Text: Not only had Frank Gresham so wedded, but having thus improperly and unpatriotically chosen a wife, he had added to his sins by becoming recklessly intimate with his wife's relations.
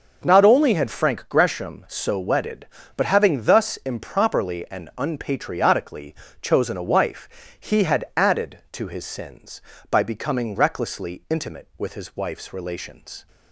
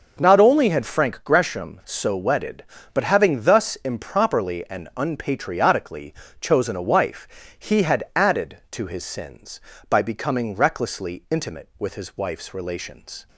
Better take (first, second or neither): neither